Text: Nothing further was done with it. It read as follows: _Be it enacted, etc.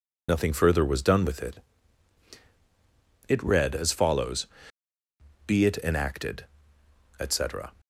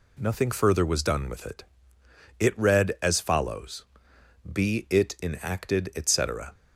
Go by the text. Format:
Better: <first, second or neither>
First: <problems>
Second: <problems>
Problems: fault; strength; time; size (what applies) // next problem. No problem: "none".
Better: second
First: loses the start of "Nothing"; at 0.2 s; 45 ms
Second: none